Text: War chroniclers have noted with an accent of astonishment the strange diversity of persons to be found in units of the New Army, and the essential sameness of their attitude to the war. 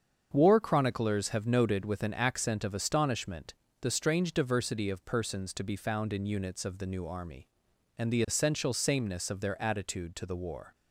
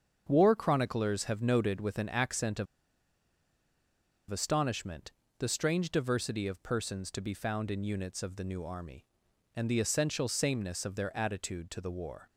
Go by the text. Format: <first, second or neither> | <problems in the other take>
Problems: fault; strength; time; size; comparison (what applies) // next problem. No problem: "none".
first | starts louder than the rest; until 1.3 s; 7 dB; also in the first // pauses between "of" and "astonishment"; strong; at 2.6 s; 1.6 s long // pauses between "astonishment" and "the"; slight; at 5.0 s; 0.30 s long; slight in the first